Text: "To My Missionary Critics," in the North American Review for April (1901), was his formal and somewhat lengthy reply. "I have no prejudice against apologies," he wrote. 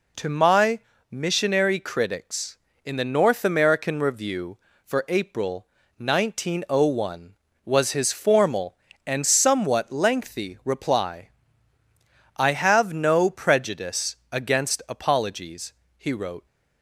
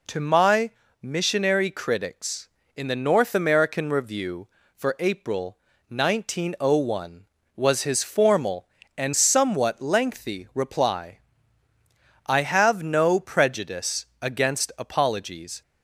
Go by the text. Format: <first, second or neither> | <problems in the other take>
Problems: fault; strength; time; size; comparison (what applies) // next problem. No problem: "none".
first | pauses between "My" and "Missionary"; slight; at 0.6 s; 0.32 s long; slight in the first // pauses between "prejudice" and "against"; slight; at 14.0 s; 0.16 s long; slight in the first // stops before "he wrote"; at 15.6 s